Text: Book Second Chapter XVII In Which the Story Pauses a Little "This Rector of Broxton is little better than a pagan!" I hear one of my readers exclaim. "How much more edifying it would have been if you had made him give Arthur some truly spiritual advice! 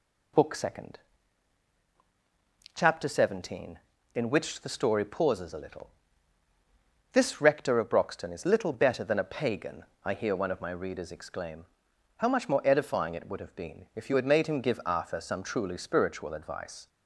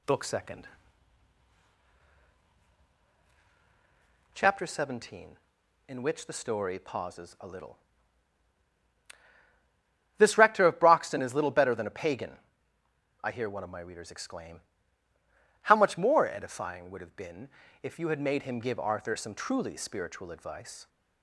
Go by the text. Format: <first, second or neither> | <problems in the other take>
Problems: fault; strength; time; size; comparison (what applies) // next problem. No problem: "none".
first | pauses between "Second" and "Chapter"; strong; at 0.6 s; 3.6 s long; strong in the first // pauses between "Little" and "This"; strong; at 7.7 s; 2.4 s long; also in the first // skips "it"; at 16.8 s // pauses between "been" and "if"; slight; at 17.4 s; 0.36 s long